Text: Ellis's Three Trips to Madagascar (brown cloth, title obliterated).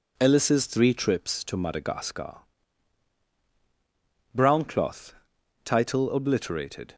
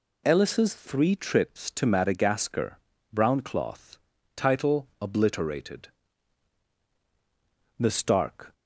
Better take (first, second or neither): first